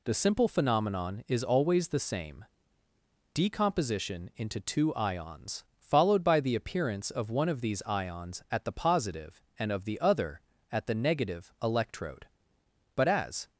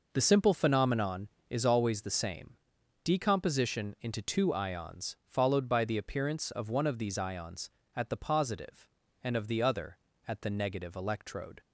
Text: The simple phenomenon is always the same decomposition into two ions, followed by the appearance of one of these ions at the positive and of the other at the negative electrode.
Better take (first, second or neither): second